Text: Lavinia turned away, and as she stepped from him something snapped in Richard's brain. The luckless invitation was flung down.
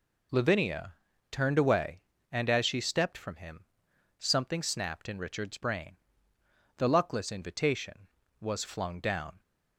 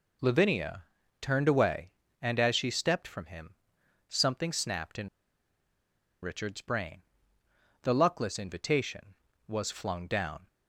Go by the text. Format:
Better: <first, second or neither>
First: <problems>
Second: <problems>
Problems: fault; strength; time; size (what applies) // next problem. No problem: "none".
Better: first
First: pauses between "Lavinia" and "turned"; at 0.9 s; 0.38 s long // pauses between "him" and "something"; noticeable; at 3.6 s; 0.56 s long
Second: pauses between "Lavinia" and "turned"; at 0.8 s; 0.38 s long // pauses between "him" and "something"; noticeable; at 3.5 s; 0.56 s long // pauses between "in" and "Richard's"; at 5.0 s; 1.1 s long